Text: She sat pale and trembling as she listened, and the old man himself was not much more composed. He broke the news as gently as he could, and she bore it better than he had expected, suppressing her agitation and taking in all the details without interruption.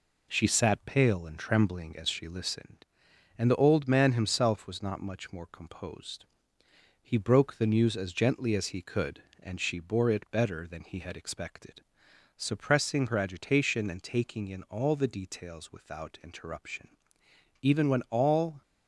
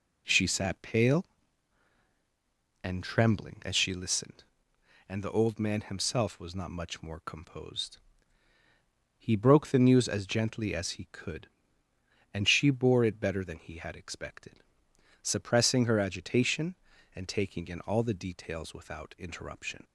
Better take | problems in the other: second | goes on to say "Even when all"; noticeable; from 17.6 s on; 0.98 s long

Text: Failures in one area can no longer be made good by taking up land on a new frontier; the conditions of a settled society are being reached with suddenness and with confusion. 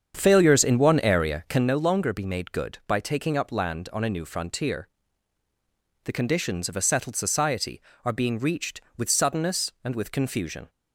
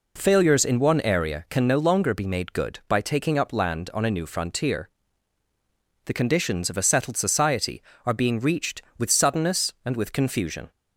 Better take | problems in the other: second | starts louder than the rest; strong; until 1.7 s; 7.5 dB

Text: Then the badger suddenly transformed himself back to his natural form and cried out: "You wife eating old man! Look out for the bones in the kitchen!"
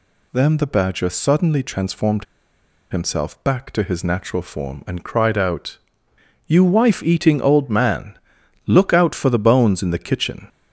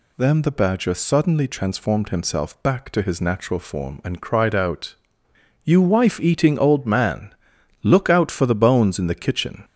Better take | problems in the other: second | pauses between "transformed" and "himself"; noticeable; at 2.2 s; 0.66 s long

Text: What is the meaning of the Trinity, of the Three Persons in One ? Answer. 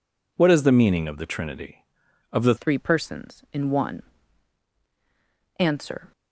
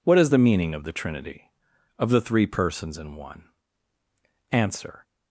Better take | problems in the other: second | changes voice at "Three"; from 2.5 s on; 3.6 s long

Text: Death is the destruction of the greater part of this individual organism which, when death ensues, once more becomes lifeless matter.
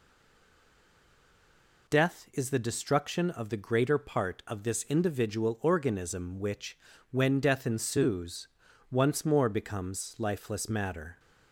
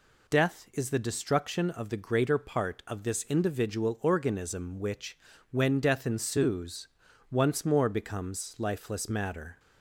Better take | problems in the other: second | stays silent before the first word; noticeable; until 1.8 s; 1.8 s long

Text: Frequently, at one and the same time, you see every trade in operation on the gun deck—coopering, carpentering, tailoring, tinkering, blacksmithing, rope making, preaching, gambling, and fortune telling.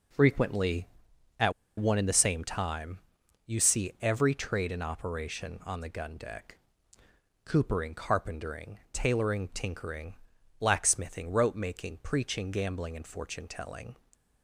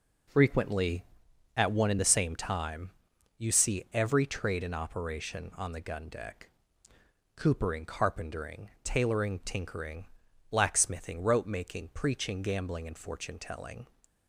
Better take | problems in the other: second | pauses between "at" and "one"; slight; at 1.5 s; 0.25 s long

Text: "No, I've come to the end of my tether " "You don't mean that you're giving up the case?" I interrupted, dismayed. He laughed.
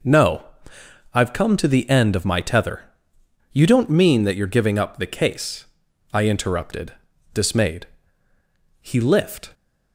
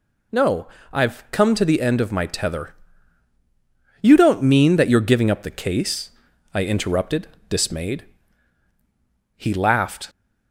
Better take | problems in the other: second | says "lift" for "laughed"; at 8.9 s

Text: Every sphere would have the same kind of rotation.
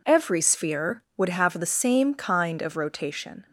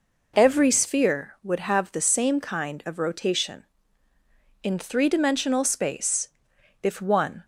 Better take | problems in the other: first | goes on to say "In three dimensional space if one"; strong; from 4.6 s on; 2.8 s long

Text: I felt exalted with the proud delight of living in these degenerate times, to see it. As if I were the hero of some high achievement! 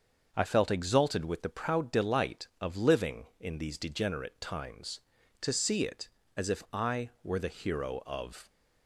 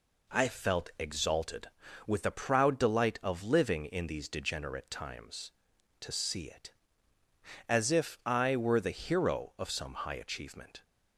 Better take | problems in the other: second | starts louder than the rest; until 1.3 s; 6.5 dB // stops before "some high achievement"; at 8.4 s

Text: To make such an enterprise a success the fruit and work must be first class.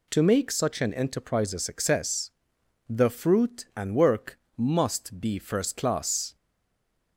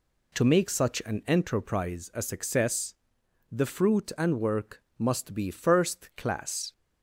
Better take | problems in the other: second | pauses between "success" and "the"; noticeable; at 2.3 s; 0.58 s long; noticeable in the second // pauses between "work" and "must"; slight; at 4.3 s; 0.18 s long; slight in the second // stays silent after the last word; slight; from 6.3 s on; 0.8 s long

